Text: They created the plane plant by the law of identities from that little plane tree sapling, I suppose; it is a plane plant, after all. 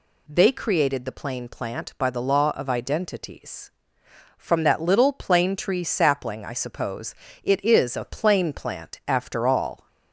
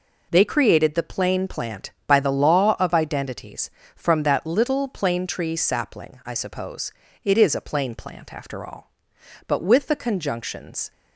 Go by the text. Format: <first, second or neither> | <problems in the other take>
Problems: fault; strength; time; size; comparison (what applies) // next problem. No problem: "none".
first | goes on to say "But with the conjunctions"; from 9.4 s on; 1.4 s long